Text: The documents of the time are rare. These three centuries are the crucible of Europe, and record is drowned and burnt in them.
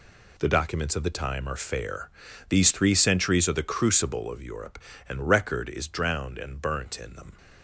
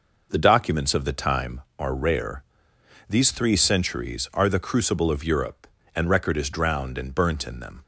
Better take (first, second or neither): second